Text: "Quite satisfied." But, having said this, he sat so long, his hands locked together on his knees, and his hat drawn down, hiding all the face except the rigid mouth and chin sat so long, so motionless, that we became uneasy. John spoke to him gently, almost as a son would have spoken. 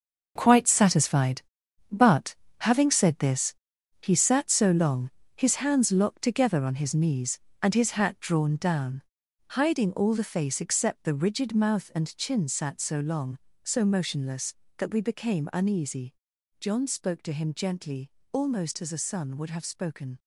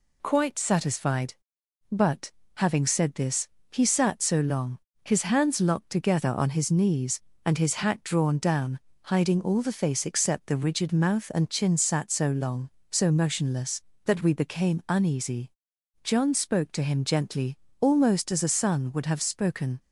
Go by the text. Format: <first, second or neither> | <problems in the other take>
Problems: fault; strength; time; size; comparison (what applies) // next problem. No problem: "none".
second | gets quieter; strong; throughout; 11 dB